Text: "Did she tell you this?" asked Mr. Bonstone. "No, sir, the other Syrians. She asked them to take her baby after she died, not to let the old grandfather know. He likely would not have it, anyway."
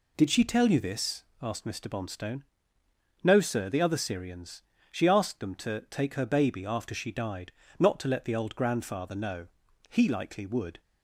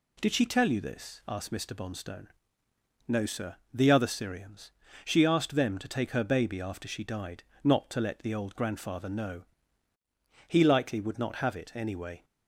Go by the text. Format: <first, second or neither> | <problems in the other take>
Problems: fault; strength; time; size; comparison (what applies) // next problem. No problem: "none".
second | stops before "not have it anyway"; at 10.7 s